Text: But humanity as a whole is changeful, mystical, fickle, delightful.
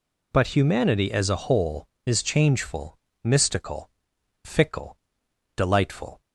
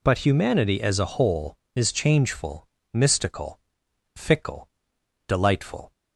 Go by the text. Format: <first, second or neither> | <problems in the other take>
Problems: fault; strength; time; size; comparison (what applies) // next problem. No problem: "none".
neither | none